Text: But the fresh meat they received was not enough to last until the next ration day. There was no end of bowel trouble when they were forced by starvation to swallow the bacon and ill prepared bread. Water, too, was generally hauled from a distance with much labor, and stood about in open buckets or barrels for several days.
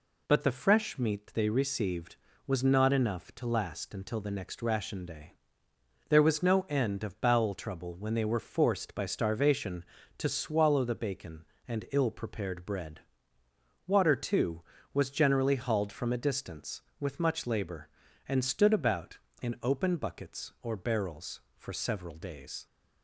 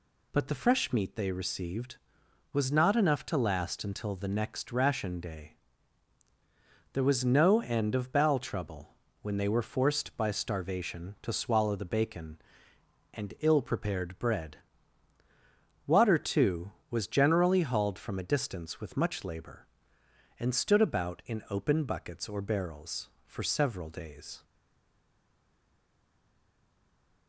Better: first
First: none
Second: pauses between "trouble" and "when"; slight; at 8.9 s; 0.28 s long // stays silent after the last word; strong; from 24.4 s on; 2.8 s long

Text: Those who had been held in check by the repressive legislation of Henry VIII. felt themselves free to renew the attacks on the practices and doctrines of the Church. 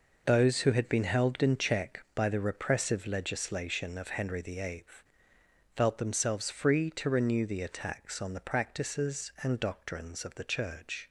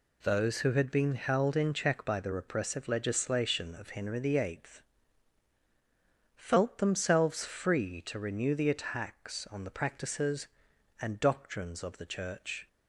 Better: neither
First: none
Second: none

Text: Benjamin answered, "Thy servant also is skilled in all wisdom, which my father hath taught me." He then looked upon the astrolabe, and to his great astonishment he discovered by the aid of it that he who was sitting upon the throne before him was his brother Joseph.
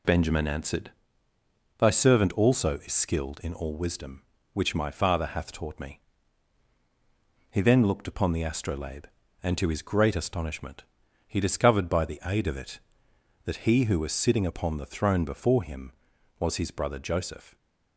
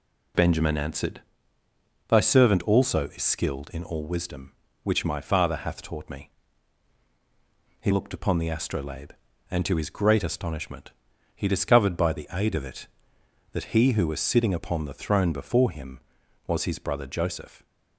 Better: first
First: pauses between "astonishment" and "he"; at 10.8 s; 0.42 s long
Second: skips "then"; at 7.9 s // pauses between "astonishment" and "he"; at 10.9 s; 0.42 s long

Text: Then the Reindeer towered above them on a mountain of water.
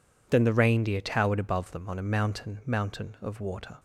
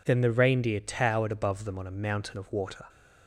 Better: second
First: says "mountain" twice; at 2.6 s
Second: none

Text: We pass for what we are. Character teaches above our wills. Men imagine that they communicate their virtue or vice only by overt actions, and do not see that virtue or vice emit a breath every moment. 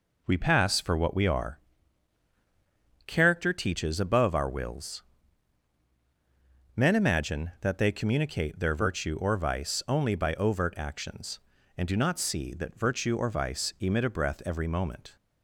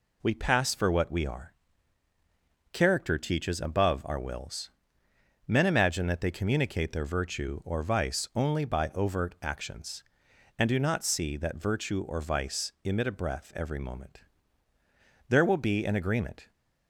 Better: first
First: none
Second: goes on to say "There will be an agreement"; noticeable; from 15.3 s on; 1.2 s long

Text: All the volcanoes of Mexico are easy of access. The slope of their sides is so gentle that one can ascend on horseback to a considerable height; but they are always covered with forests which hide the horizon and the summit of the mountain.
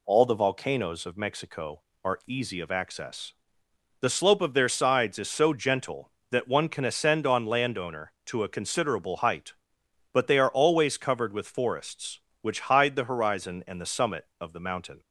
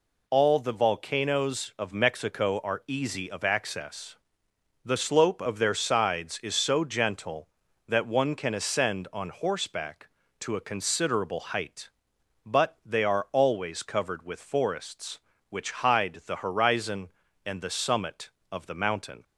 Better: second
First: says "landowner" for "horseback"; at 7.4 s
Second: none

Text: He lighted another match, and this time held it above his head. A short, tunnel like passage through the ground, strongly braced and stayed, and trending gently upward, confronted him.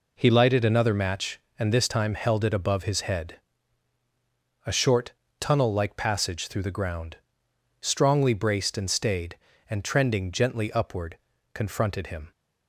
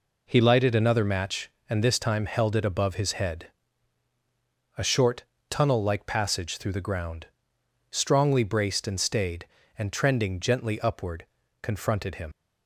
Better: first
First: none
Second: leaves "him" unfinished; at 12.3 s; 80 ms

